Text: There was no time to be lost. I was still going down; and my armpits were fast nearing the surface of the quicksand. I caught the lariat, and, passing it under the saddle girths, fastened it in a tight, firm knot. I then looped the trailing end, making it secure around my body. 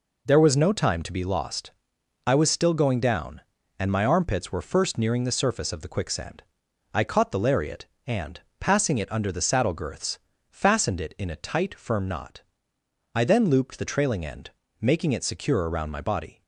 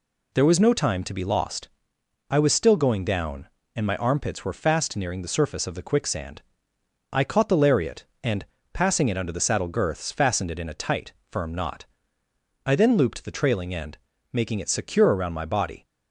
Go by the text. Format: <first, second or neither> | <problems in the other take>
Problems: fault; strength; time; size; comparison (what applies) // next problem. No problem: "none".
second | says "first" for "fast"; at 4.6 s